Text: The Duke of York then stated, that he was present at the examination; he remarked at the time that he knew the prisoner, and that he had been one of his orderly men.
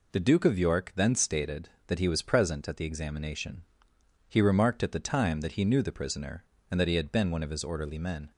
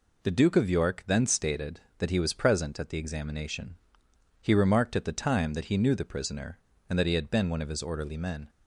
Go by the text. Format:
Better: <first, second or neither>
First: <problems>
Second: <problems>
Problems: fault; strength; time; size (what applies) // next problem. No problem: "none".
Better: neither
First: none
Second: none